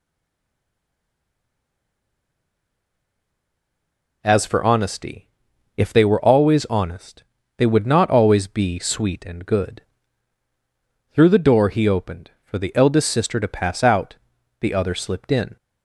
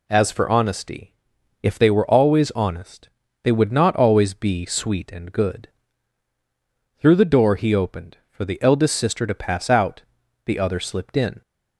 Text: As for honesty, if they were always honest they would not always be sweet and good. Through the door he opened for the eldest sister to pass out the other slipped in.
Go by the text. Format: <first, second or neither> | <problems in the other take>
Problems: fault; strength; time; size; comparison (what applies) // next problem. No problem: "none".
second | stays silent before the first word; strong; until 4.2 s; 4.2 s long // pauses between "honest" and "they"; slight; at 7.2 s; 0.34 s long; slight in the second // pauses between "out" and "the"; at 14.1 s; 0.44 s long; also in the second